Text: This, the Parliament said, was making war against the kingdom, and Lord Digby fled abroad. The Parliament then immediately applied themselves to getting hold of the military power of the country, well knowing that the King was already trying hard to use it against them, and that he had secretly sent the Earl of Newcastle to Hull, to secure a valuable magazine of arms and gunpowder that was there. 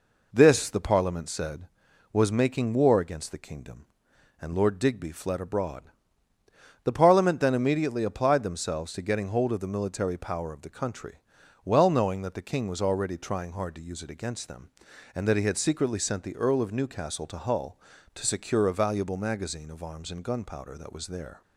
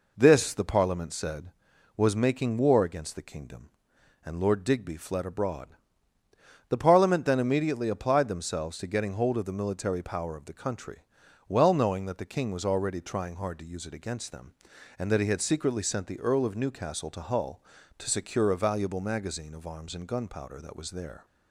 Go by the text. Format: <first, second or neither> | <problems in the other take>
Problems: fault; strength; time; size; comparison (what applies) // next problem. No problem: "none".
neither | none